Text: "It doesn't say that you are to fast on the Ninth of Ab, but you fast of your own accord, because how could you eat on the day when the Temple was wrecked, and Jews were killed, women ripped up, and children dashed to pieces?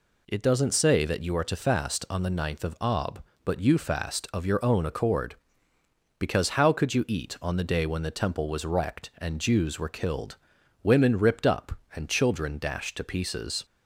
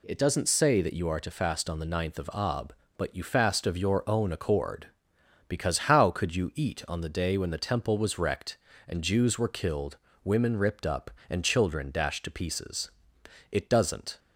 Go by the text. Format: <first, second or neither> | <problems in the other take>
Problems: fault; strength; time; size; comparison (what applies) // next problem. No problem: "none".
first | goes on to say "It doesn't"; noticeable; from 13.5 s on; 0.68 s long